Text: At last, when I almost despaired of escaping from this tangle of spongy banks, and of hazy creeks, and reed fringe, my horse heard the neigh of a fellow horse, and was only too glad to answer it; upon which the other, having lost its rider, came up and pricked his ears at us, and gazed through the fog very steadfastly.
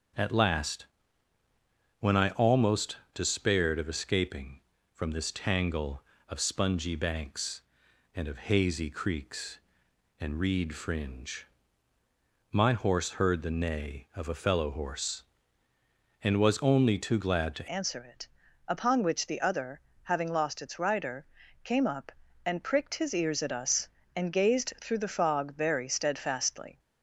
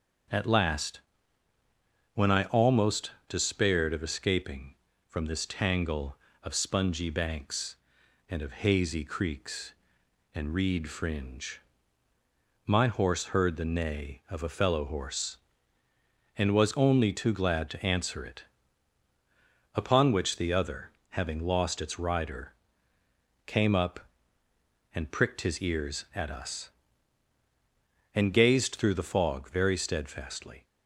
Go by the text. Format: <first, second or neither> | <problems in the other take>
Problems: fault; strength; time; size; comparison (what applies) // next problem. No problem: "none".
second | starts louder than the rest; until 2.3 s; 6.5 dB; also in the second // pauses between "almost" and "despaired"; slight; at 2.9 s; 0.18 s long; slight in the second // changes voice at "answer"; from 17.7 s on; 9.0 s long